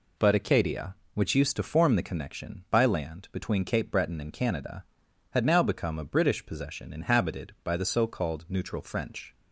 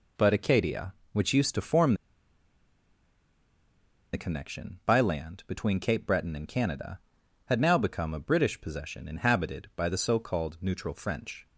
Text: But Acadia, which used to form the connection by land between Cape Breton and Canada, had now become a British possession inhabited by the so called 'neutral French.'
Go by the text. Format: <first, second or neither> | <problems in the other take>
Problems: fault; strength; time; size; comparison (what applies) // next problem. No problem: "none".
first | pauses between "form" and "the"; strong; at 1.9 s; 2.1 s long